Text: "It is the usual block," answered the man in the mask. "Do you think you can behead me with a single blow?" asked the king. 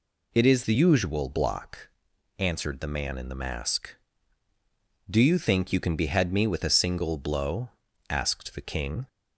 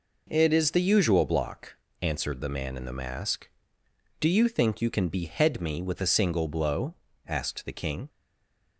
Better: first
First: none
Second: stays silent after the last word; slight; from 8.0 s on; 0.7 s long

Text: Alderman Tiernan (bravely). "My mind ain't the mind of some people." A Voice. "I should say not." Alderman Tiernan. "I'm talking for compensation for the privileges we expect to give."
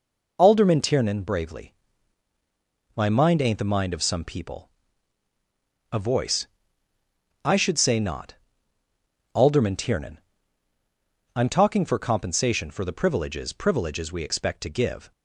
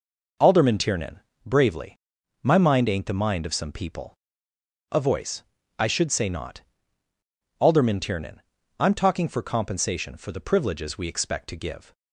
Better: second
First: says "privileges" twice; at 13.5 s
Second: none

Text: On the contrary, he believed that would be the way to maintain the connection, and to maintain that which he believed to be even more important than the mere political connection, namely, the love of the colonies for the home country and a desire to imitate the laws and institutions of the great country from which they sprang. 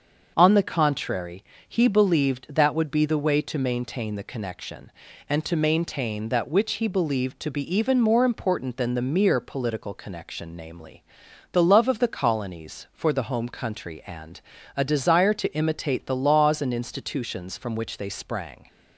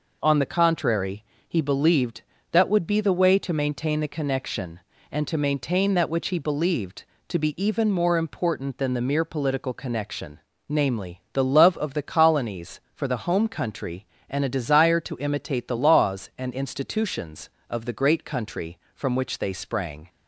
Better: second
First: starts louder than the rest; until 1.3 s; 6.5 dB // pauses between "and" and "a"; at 14.3 s; 0.38 s long // skips "of the great country"; at 17.5 s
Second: none

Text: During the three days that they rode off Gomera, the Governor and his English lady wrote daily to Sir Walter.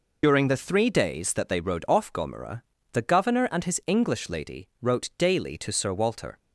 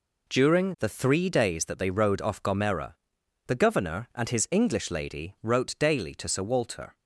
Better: second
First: loses the start of "During"; at 0.2 s; 85 ms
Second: none

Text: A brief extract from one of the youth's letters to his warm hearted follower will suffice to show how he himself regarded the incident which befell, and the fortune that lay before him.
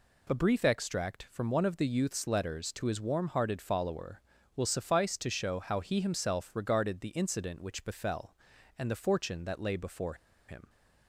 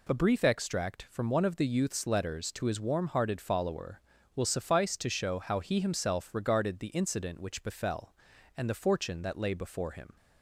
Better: second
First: pauses between "before" and "him"; slight; at 10.1 s; 0.34 s long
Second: none

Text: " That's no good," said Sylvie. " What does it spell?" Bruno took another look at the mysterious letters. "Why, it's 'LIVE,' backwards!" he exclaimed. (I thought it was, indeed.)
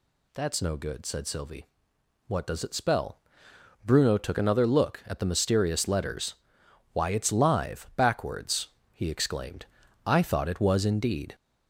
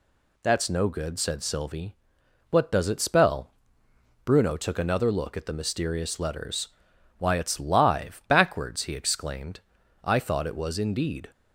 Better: second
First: gets louder; strong; throughout; 9 dB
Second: none

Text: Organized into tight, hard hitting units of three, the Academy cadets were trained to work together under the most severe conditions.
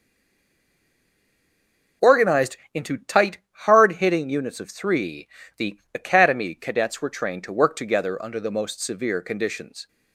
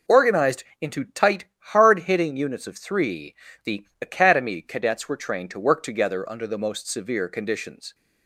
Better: second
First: stays silent before the first word; noticeable; until 2.0 s; 2.0 s long // pauses between "Organized" and "into"; slight; at 2.5 s; 0.18 s long // pauses between "the" and "Academy"; slight; at 5.7 s; 0.16 s long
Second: pauses between "Organized" and "into"; slight; at 0.6 s; 0.18 s long // pauses between "the" and "Academy"; slight; at 3.8 s; 0.16 s long

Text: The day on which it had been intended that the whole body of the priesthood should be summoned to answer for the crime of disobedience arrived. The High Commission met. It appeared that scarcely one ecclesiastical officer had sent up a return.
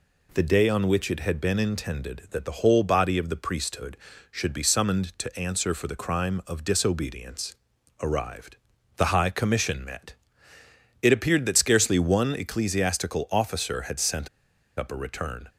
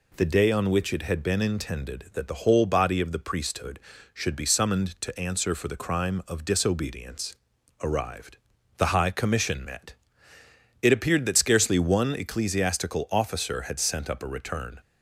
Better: second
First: pauses between "disobedience" and "arrived"; at 7.5 s; 0.44 s long // pauses between "sent" and "up"; noticeable; at 14.2 s; 0.50 s long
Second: pauses between "disobedience" and "arrived"; at 7.3 s; 0.44 s long

